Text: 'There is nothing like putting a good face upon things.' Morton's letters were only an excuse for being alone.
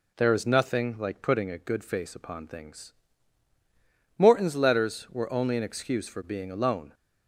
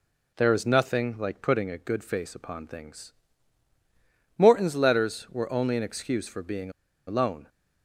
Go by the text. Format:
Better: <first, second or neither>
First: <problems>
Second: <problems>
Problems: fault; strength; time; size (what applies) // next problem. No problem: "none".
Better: first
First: none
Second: pauses between "being" and "alone"; slight; at 6.7 s; 0.36 s long